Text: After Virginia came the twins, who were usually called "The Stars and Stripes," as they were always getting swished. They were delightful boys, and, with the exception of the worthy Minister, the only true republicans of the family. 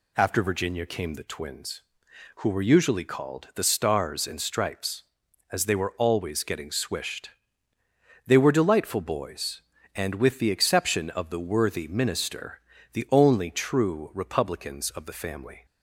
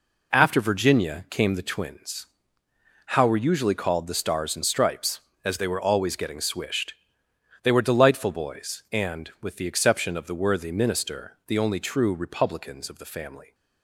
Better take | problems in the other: first | says "how" for "who"; at 3.0 s

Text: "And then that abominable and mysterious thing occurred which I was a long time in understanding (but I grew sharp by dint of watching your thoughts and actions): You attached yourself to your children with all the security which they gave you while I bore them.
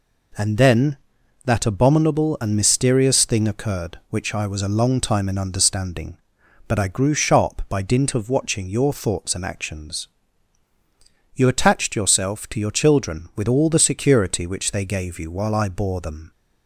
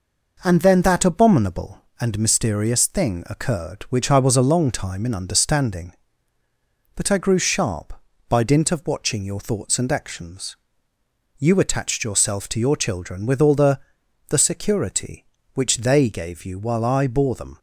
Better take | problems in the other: first | says "the" twice; at 14.2 s

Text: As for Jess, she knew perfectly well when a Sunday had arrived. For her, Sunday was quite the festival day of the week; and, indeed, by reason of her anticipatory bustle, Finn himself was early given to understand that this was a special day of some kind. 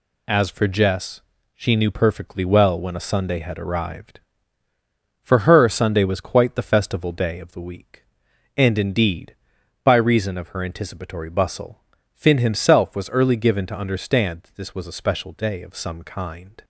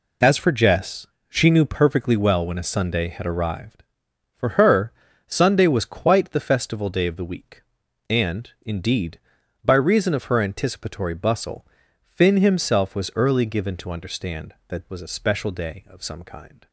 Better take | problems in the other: first | skips "this"; at 14.9 s

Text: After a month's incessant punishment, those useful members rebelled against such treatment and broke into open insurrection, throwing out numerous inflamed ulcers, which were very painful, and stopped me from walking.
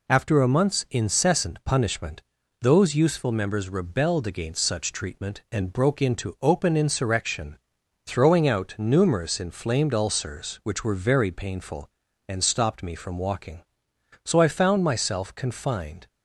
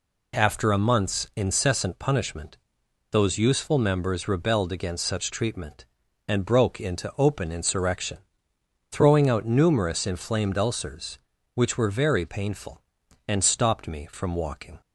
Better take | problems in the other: second | goes on to say "So I found myself confined"; strong; from 14.2 s on; 1.8 s long

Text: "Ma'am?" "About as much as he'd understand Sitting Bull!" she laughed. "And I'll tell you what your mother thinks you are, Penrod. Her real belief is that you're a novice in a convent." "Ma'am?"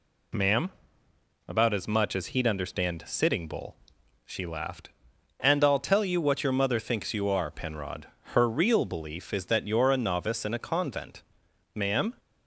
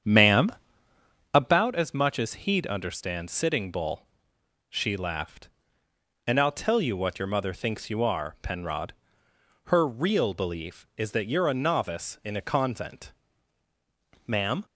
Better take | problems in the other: first | starts louder than the rest; strong; until 1.6 s; 8.5 dB

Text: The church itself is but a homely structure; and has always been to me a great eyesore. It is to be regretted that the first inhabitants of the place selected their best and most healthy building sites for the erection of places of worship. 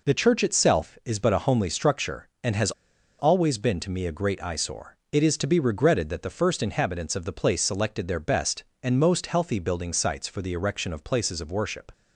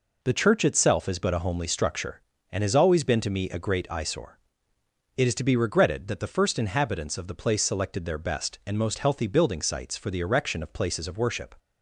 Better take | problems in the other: second | pauses between "has" and "always"; noticeable; at 2.7 s; 0.47 s long

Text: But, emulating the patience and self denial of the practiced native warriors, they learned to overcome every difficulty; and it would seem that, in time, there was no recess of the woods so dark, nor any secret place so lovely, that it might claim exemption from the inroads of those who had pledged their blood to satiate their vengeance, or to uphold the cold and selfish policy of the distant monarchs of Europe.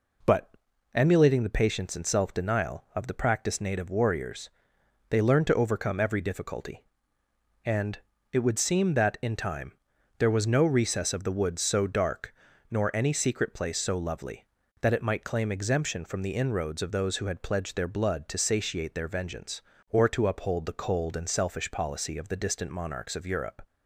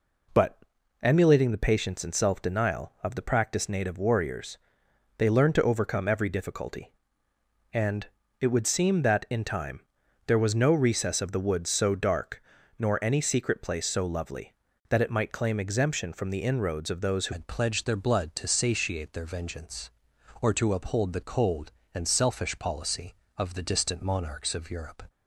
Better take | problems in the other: first | pauses between "and" and "it"; slight; at 8.0 s; 0.34 s long; slight in the first // changes voice at "had"; from 17.3 s on; 7.7 s long

